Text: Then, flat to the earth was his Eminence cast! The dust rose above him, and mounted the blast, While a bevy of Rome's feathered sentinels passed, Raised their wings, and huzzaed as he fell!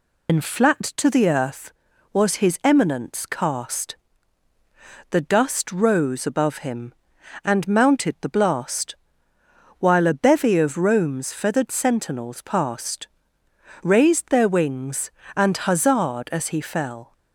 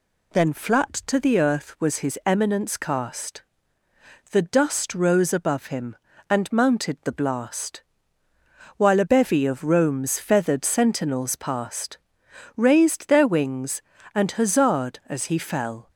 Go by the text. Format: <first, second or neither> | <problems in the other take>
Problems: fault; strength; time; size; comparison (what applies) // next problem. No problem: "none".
second | loses the start of "Then"; at 0.2 s; 105 ms